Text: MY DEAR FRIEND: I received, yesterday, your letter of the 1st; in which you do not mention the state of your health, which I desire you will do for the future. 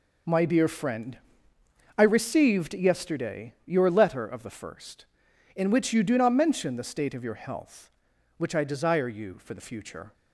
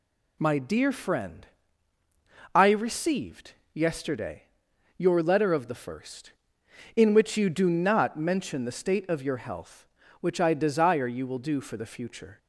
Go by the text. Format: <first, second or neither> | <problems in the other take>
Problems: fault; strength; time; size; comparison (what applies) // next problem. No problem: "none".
second | skips "will do"; at 9.3 s